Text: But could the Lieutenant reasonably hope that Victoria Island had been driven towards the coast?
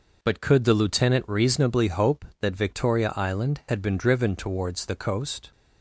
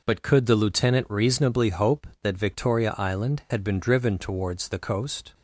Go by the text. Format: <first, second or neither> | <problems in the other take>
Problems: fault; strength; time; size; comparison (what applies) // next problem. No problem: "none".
neither | none